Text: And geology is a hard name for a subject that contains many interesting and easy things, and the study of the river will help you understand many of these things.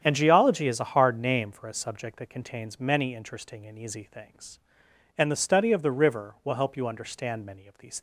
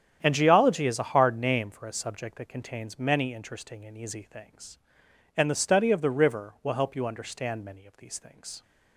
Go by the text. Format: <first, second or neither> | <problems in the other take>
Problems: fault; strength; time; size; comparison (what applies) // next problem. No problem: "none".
second | starts louder than the rest; strong; until 1.0 s; 9 dB; strong in the second // stops before "things"; at 7.9 s